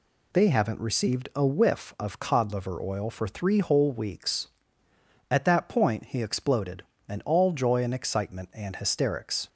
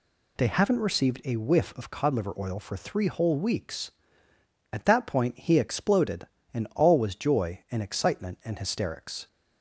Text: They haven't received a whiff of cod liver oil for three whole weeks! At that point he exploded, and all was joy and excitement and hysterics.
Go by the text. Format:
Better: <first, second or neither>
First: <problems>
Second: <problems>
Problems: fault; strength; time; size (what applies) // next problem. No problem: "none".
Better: second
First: skips "was"; at 7.5 s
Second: none